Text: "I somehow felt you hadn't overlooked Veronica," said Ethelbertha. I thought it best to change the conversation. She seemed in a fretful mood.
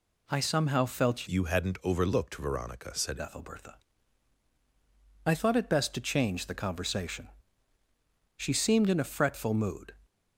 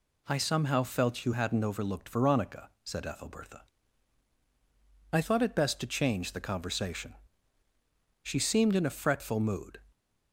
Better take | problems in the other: second | changes voice from "you" to "said"; from 1.2 to 3.2 s; 2.0 s long

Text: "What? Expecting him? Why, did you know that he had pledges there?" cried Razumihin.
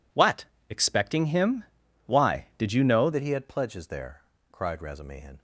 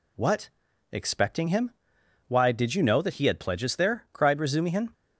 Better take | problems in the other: second | changes voice at "that"; from 3.1 s on; 2.2 s long

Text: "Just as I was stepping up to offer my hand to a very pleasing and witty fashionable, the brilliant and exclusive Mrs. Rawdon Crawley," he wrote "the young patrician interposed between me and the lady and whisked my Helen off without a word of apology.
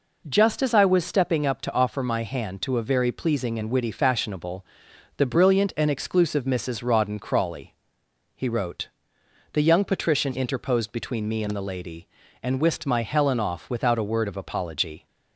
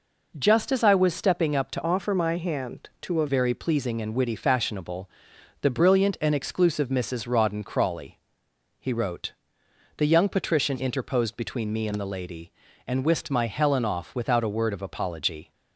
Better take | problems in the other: first | changes voice from "offer" to "a"; from 1.8 to 3.2 s; 1.4 s long // pauses between "wrote" and "the"; noticeable; at 9.3 s; 0.66 s long; noticeable in the first

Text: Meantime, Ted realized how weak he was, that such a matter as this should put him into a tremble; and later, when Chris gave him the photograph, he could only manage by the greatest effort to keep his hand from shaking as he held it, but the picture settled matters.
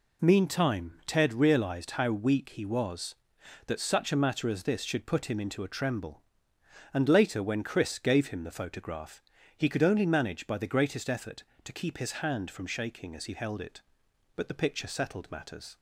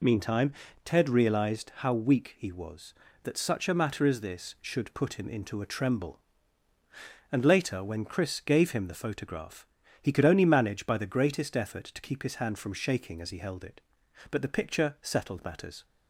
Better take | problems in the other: neither | none

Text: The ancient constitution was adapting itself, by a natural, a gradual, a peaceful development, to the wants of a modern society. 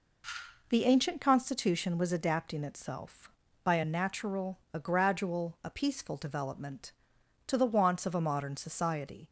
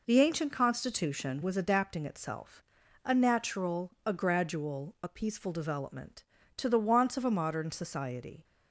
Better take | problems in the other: first | skips "by"; at 2.8 s

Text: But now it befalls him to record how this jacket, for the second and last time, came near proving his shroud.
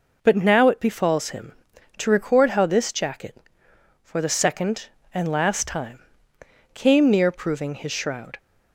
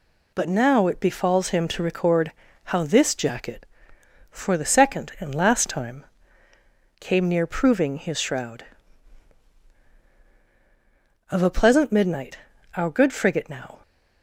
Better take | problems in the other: first | pauses between "record" and "how"; slight; at 2.3 s; 0.34 s long // goes on to say "Of a pleasant midnight our good frigate now"; strong; from 11.3 s on; 2.5 s long

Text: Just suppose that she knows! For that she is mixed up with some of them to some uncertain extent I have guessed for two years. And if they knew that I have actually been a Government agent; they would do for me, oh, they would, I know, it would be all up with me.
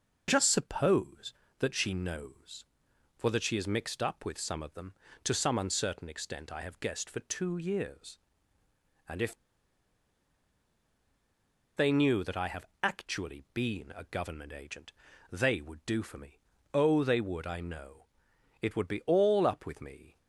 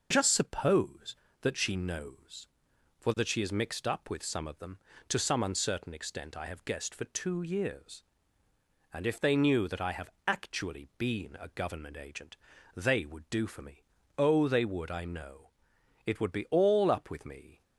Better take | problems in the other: second | pauses between "if" and "they"; strong; at 9.3 s; 2.4 s long // pauses between "have" and "actually"; slight; at 12.6 s; 0.16 s long; slight in the second

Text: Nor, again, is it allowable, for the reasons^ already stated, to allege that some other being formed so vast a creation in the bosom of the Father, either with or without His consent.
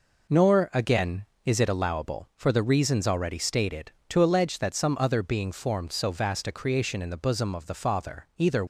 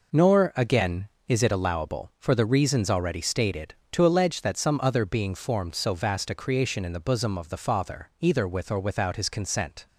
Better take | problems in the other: second | stops before "with or without His consent"; at 8.6 s

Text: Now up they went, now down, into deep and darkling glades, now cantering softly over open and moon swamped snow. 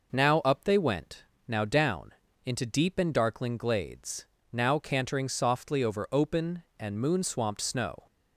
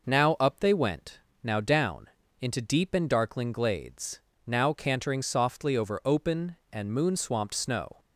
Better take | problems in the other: neither | none

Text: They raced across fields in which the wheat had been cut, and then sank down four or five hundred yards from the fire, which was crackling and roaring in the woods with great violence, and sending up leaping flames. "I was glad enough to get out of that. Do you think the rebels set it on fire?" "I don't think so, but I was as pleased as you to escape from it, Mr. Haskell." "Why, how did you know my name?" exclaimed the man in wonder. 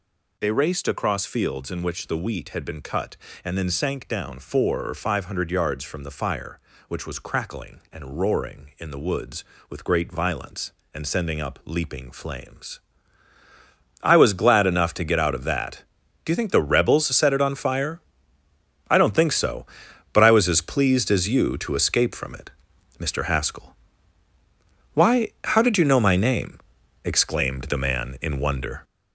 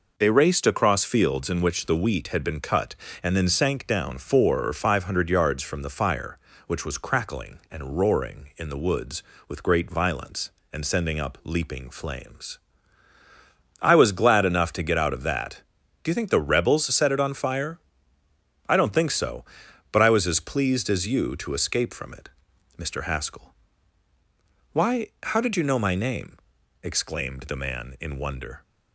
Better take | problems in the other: second | gets louder; throughout; 6.5 dB

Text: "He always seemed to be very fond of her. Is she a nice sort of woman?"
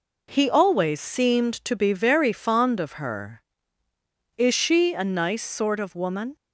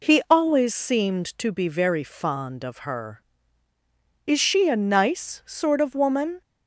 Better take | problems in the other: neither | none

